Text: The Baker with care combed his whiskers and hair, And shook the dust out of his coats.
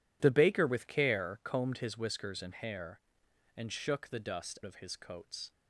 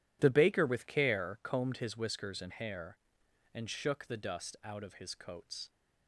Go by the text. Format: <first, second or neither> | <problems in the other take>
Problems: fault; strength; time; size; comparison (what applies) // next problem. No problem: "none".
second | skips "out"; at 4.6 s